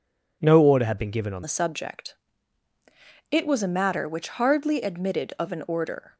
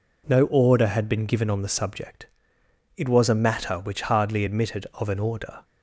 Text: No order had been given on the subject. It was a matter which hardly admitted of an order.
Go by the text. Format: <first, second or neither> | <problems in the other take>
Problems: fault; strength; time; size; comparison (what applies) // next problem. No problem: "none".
second | changes voice at "the"; from 1.4 s on; 4.7 s long